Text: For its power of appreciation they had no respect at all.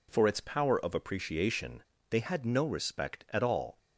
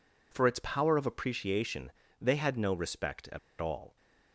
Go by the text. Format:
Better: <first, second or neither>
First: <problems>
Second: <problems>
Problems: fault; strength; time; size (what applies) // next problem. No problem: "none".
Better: first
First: pauses between "appreciation" and "they"; slight; at 1.8 s; 0.26 s long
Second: pauses between "appreciation" and "they"; slight; at 1.9 s; 0.26 s long // pauses between "at" and "all"; slight; at 3.3 s; 0.22 s long